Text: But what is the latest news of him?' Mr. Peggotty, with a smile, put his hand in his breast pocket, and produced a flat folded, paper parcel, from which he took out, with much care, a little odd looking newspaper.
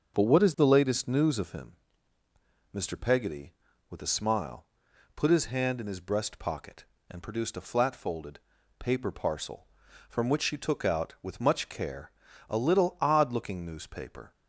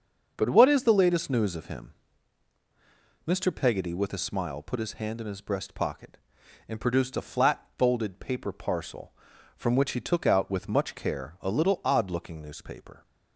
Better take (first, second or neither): second